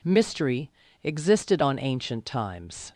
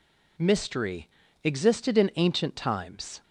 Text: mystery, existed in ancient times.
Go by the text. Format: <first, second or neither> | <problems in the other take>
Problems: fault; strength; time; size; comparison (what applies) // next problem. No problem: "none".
second | says "on" for "in"; at 1.6 s